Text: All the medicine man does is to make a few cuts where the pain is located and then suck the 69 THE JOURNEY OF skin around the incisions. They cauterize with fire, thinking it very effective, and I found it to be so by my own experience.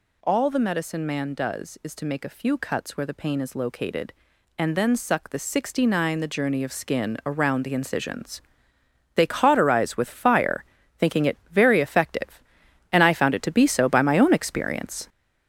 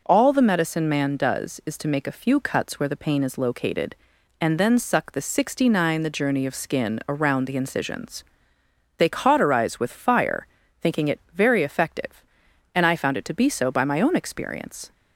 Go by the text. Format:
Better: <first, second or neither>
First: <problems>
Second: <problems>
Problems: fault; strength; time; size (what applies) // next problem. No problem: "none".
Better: second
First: gets louder; noticeable; throughout; 6 dB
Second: none